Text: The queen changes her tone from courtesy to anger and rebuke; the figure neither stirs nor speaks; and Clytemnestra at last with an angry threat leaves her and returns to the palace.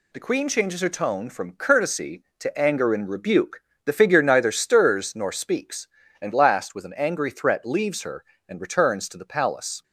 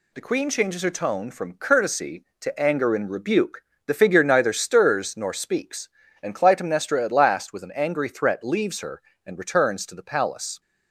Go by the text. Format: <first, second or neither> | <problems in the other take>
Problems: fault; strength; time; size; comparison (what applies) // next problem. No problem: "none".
second | skips "Clytemnestra at"; at 6.3 s